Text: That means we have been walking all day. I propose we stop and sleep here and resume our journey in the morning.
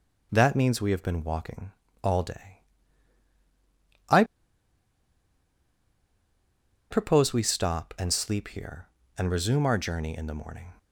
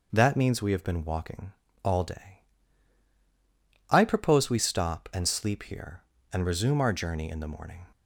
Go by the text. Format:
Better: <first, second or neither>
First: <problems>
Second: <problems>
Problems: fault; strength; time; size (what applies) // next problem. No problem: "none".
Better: second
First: pauses between "walking" and "all"; slight; at 1.7 s; 0.32 s long // pauses between "I" and "propose"; strong; at 4.2 s; 2.6 s long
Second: pauses between "walking" and "all"; slight; at 1.5 s; 0.32 s long